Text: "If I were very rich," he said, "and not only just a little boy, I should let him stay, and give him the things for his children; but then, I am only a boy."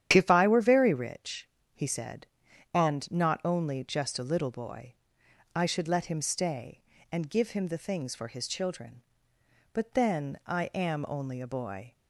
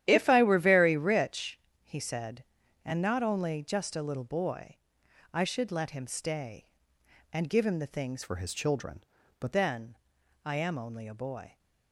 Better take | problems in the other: first | starts louder than the rest; strong; until 1.0 s; 11.5 dB; strong in the first // changes voice from "for" to "but"; from 8.2 to 9.5 s; 1.3 s long

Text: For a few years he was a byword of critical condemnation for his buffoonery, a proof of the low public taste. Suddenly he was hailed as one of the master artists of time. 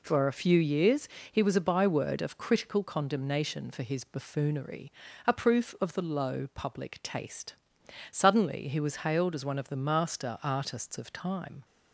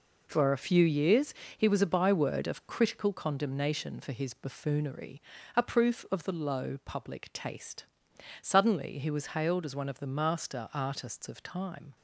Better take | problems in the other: first | gets quieter; strong; throughout; 8 dB // pauses between "years" and "he"; slight; at 1.3 s; 0.22 s long; slight in the first

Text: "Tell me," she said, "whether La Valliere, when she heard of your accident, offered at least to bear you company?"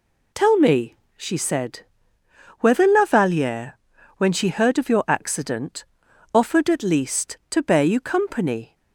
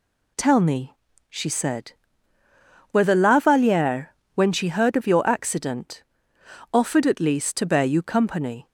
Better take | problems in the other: neither | none

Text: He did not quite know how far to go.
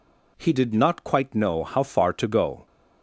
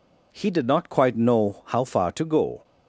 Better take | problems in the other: neither | none

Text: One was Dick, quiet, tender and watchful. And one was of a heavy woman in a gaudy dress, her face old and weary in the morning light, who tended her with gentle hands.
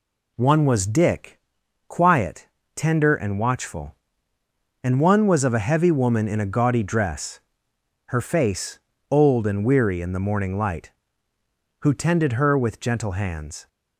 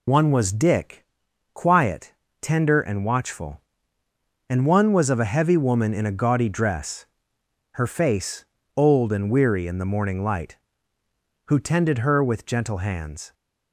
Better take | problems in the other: first | loses the start of "One"; at 0.0 s; 60 ms // pauses between "face" and "old"; slight; at 8.4 s; 0.32 s long; slight in the first

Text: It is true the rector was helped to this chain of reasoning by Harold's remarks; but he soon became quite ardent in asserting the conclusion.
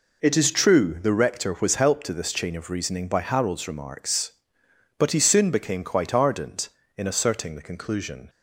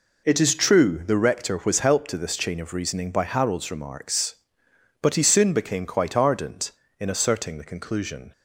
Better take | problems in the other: neither | none

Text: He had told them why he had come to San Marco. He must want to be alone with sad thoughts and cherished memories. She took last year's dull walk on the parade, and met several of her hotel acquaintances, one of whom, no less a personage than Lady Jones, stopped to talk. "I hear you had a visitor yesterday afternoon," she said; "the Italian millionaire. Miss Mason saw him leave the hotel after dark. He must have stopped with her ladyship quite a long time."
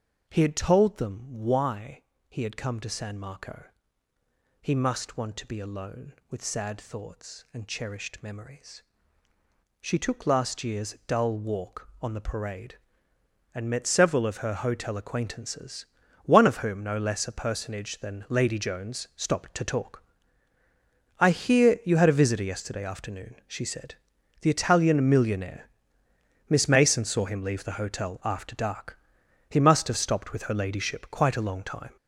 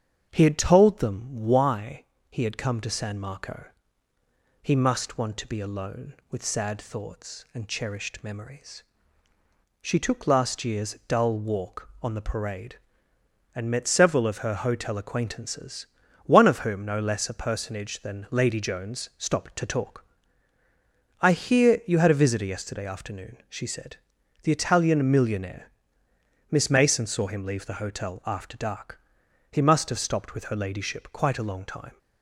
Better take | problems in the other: second | gets louder; strong; throughout; 7 dB // starts louder than the rest; until 1.3 s; 6.5 dB; strong in the second // pauses between "why" and "he"; slight; at 2.0 s; 0.26 s long; slight in the second

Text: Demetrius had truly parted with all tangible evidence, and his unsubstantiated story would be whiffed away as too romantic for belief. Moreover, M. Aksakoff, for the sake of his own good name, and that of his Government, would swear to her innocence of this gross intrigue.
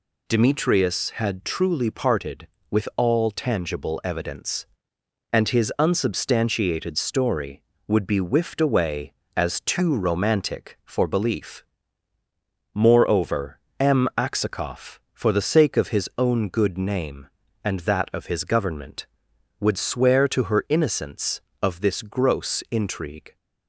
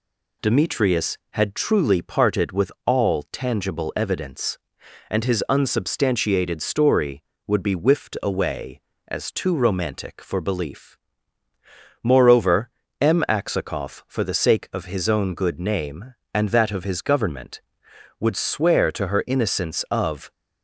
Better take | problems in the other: first | stops before "this gross intrigue"; at 20.3 s

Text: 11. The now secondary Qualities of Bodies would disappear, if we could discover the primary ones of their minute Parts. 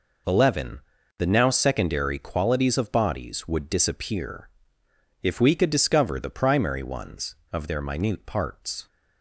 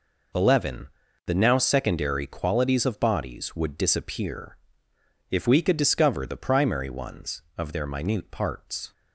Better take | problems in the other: neither | none

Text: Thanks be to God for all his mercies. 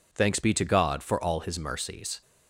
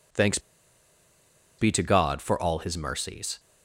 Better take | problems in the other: first | pauses between "Thanks" and "be"; at 0.3 s; 1.2 s long

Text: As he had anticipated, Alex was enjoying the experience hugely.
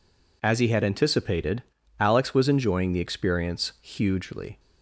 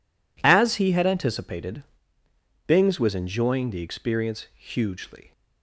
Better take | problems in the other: first | says "Bings" for "Alex"; at 2.6 s

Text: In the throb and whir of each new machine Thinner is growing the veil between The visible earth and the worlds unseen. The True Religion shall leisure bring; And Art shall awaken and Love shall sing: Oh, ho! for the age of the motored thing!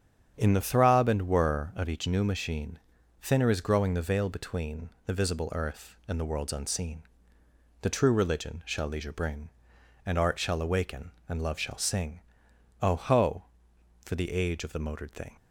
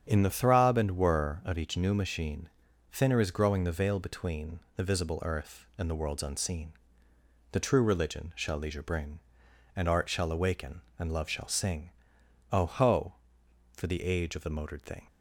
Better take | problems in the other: neither | starts louder than the rest; strong; the same in both // pauses between "machine" and "Thinner"; the same in both // pauses between "between" and "The"; slight; the same in both

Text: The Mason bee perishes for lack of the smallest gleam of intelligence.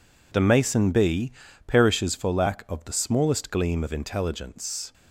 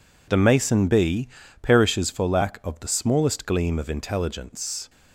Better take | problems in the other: neither | pauses between "bee" and "perishes"; slight; the same in both

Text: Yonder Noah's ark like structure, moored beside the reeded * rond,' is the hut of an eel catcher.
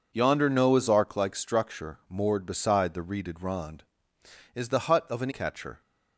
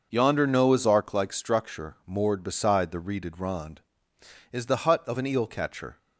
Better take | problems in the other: second | skips "eel"; at 5.3 s

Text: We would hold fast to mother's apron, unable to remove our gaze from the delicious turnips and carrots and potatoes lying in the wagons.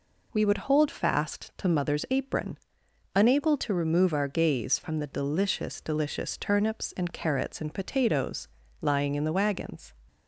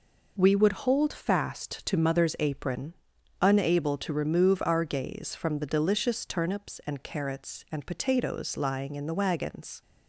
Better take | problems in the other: second | says "delicious" twice; at 5.7 s // pauses between "potatoes" and "lying"; slight; at 8.4 s; 0.34 s long

